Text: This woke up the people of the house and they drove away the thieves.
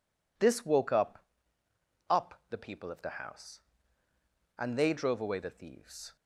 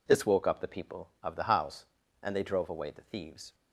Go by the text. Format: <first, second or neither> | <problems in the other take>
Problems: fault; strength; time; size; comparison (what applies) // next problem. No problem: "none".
second | says "up" twice; at 2.0 s